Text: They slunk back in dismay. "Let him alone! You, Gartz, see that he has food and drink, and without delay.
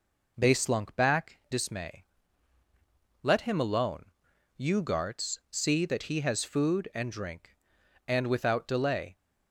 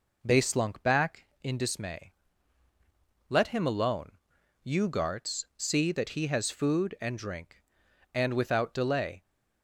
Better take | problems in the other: second | skips "in"; at 1.4 s

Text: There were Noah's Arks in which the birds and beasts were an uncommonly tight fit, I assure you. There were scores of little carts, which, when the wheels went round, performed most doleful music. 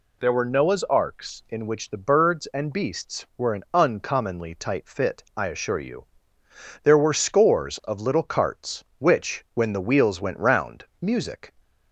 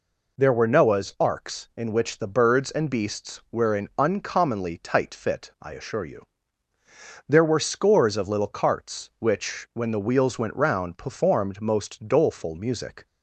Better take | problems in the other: second | skips "performed most doleful"; at 10.9 s

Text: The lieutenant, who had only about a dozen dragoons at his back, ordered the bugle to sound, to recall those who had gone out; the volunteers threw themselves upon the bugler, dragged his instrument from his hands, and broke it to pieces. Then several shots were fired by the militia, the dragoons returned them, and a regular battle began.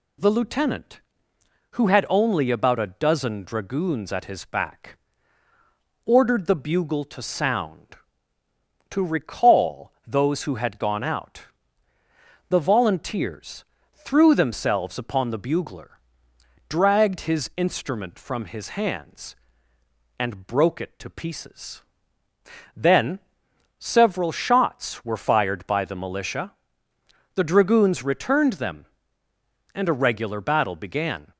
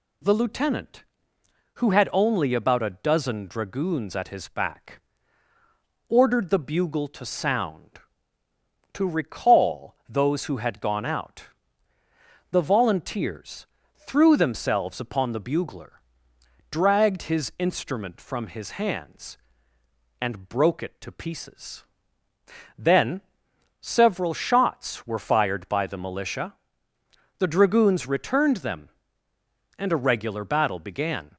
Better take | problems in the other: neither | pauses between "volunteers" and "threw"; slight; the same in both // pauses between "Then" and "several"; noticeable; the same in both

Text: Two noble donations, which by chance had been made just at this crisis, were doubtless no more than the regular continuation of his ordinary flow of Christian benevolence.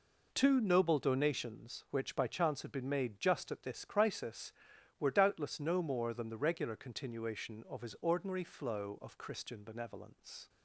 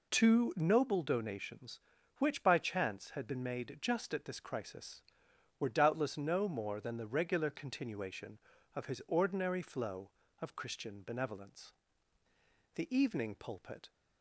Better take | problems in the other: first | goes on to say "The Evening Pulpit"; noticeable; from 12.7 s on; 1.1 s long

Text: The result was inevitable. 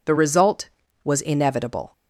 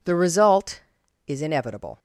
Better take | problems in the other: first | says "is" for "was"; at 1.2 s

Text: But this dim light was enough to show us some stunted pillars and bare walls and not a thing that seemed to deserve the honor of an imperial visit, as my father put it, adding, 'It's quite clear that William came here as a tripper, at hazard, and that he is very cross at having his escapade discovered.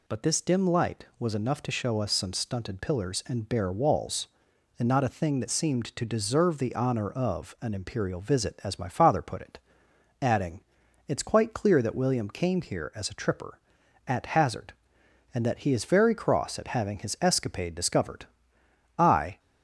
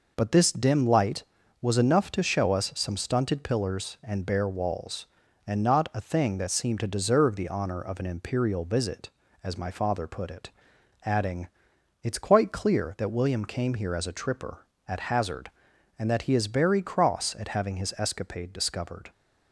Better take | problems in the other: second | goes on to say "I"; slight; from 18.9 s on; 0.42 s long

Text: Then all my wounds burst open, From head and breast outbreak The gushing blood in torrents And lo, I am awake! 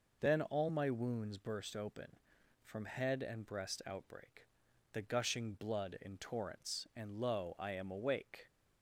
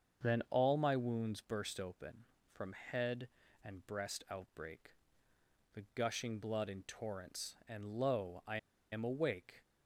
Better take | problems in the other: first | starts louder than the rest; until 1.3 s; 7 dB // pauses between "outbreak" and "The"; noticeable; at 4.9 s; 0.82 s long; noticeable in the first // pauses between "I" and "am"; slight; at 8.5 s; 0.34 s long

